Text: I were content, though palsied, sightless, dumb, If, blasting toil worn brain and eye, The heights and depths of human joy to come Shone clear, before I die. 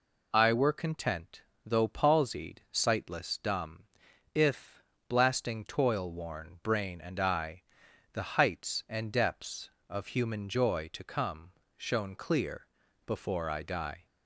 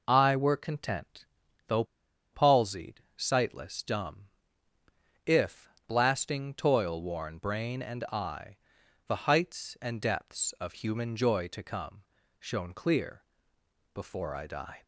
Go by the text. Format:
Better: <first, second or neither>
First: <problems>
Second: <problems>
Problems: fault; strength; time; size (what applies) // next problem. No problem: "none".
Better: first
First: pauses between "come" and "Shone"; slight; at 11.5 s; 0.24 s long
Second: pauses between "though" and "palsied"; noticeable; at 1.8 s; 0.48 s long // pauses between "come" and "Shone"; at 12.0 s; 0.38 s long